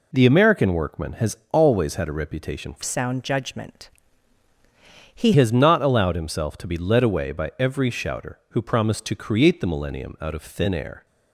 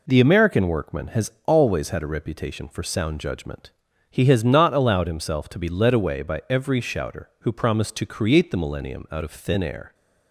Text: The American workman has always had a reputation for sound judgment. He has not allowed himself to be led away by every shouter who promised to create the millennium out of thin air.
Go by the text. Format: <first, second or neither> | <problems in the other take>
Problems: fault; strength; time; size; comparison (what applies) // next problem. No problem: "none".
second | changes voice from "sound" to "He"; from 2.8 to 5.3 s; 2.5 s long